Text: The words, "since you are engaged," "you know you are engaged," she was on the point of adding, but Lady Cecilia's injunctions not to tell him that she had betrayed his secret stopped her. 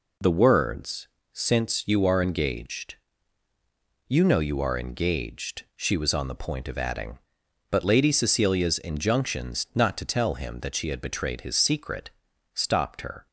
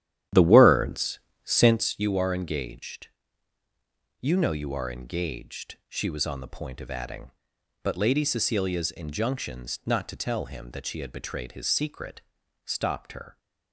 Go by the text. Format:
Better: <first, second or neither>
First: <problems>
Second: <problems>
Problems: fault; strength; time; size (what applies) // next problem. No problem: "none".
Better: first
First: pauses between "secret" and "stopped"; at 12.1 s; 0.44 s long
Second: starts louder than the rest; strong; until 2.0 s; 11 dB // pauses between "secret" and "stopped"; at 12.2 s; 0.44 s long